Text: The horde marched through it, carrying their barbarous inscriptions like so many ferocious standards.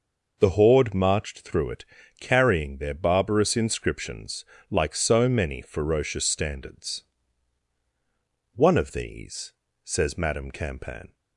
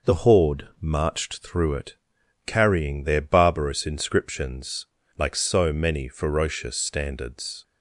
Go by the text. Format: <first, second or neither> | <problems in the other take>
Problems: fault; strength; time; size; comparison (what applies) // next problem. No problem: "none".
second | pauses between "inscriptions" and "like"; slight; at 4.4 s; 0.26 s long; slight in the second // goes on to say "One of these says Madame Campan"; strong; from 8.5 s on; 2.6 s long